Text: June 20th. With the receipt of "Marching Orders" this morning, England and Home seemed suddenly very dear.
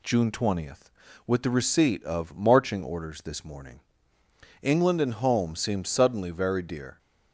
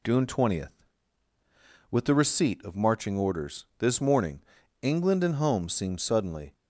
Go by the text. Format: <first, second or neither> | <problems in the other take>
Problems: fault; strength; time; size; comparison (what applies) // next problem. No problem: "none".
first | stops before "very dear"; at 6.5 s